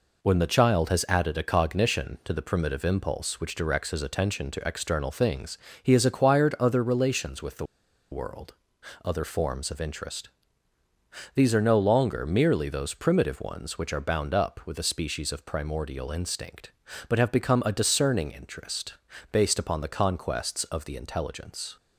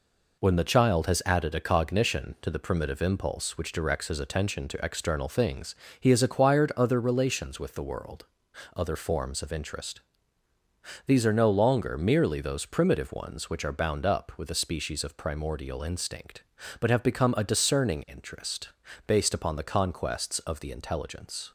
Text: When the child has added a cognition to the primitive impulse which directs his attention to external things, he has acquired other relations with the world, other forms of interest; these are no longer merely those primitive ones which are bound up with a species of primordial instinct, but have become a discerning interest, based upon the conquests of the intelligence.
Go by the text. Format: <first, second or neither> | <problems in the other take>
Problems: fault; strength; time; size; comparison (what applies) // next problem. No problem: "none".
second | pauses between "the" and "world"; noticeable; at 7.6 s; 0.46 s long